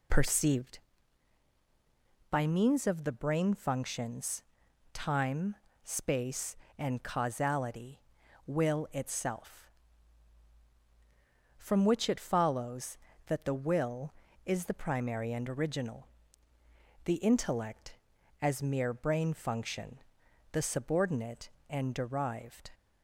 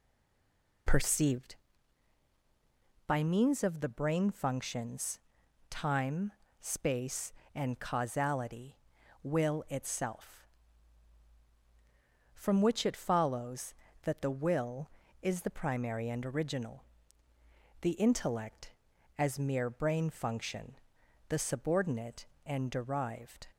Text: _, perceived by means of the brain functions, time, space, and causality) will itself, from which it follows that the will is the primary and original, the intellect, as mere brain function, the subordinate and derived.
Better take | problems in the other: first | stays silent before the first word; slight; until 0.8 s; 0.8 s long

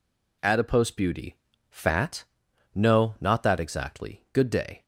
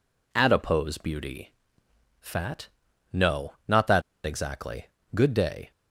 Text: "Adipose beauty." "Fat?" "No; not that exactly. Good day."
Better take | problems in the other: first | pauses between "that" and "exactly"; slight; at 4.0 s; 0.24 s long

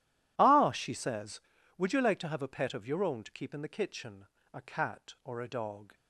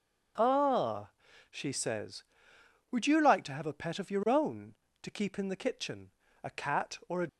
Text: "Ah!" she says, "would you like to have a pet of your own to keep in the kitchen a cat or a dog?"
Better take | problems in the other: first | pauses between "kitchen" and "a"; slight; at 6.1 s; 0.34 s long; slight in the first // stops before "dog"; at 7.2 s

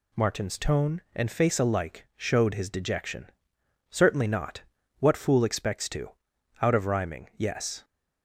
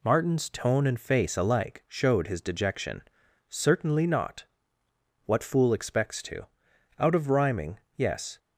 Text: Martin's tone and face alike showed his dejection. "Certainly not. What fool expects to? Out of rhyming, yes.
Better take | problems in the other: neither | none

